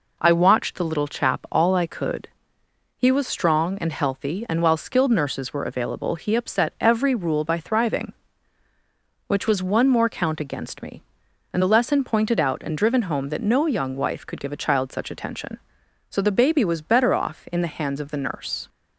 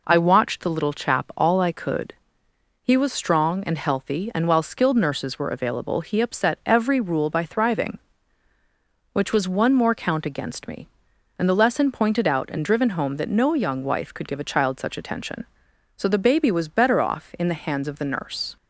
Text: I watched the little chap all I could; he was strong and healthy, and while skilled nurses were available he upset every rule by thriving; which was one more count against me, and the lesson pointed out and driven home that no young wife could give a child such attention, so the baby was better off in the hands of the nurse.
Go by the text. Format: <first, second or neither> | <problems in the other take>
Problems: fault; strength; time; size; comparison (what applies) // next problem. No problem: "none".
neither | none